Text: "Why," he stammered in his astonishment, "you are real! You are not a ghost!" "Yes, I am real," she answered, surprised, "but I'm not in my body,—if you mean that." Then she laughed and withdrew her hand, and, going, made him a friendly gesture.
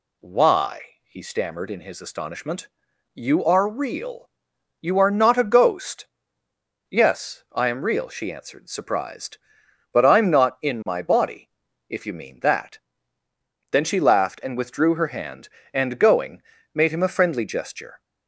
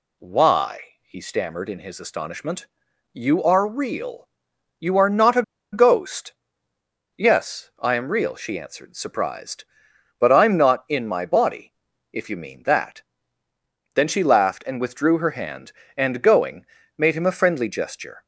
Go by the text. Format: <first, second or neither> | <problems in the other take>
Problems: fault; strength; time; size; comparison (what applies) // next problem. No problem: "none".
first | pauses between "a" and "ghost"; slight; at 5.4 s; 0.30 s long